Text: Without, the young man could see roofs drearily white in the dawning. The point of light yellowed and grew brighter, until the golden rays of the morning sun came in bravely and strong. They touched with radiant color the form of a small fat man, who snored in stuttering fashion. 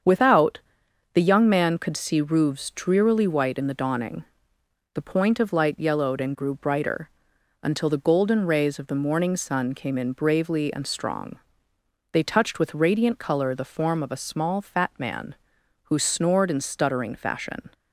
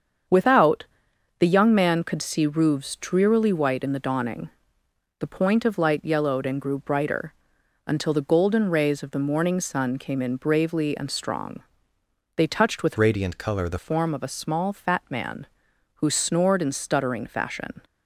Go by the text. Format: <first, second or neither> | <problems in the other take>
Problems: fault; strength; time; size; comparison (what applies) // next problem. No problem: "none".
first | starts louder than the rest; strong; until 1.8 s; 7.5 dB; strong in the first // changes voice from "radiant" to "the"; from 12.9 to 13.7 s; 0.8 s long